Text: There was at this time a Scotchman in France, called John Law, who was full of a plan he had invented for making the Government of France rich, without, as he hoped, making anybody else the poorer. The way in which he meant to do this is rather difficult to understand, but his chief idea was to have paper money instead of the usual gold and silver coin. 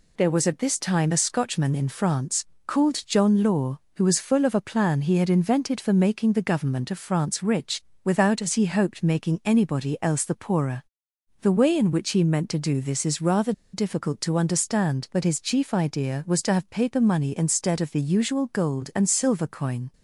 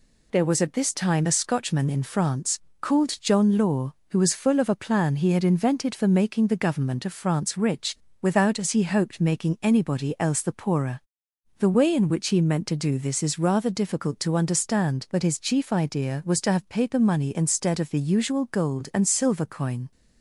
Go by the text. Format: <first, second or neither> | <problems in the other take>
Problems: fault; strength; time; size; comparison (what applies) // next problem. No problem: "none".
second | pauses between "rather" and "difficult"; slight; at 13.5 s; 0.21 s long